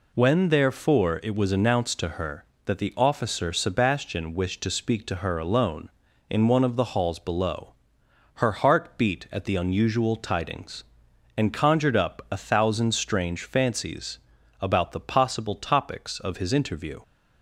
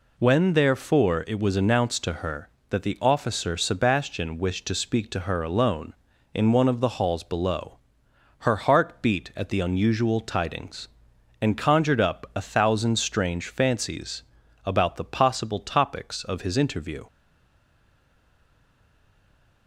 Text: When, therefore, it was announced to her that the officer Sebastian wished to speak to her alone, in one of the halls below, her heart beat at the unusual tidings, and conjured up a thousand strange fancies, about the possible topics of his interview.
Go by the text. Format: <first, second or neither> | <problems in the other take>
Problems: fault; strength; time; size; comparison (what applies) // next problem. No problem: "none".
first | stays silent after the last word; strong; from 17.0 s on; 2.6 s long